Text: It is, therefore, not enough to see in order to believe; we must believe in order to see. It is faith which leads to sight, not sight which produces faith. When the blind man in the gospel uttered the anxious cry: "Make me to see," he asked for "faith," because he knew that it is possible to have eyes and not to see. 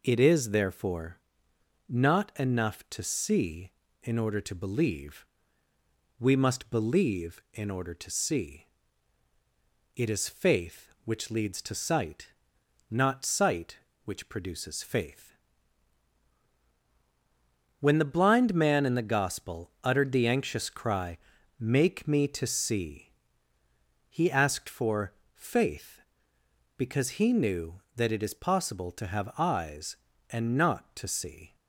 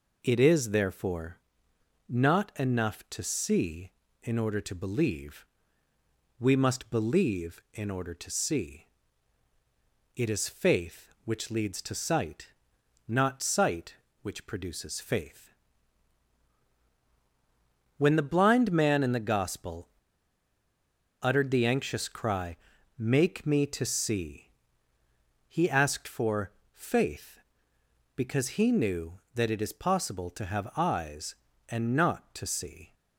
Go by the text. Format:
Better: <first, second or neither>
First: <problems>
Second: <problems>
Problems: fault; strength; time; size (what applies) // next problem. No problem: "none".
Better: first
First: pauses between "for" and "faith"; slight; at 25.1 s; 0.18 s long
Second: pauses between "gospel" and "uttered"; strong; at 19.8 s; 1.3 s long // pauses between "for" and "faith"; slight; at 26.5 s; 0.18 s long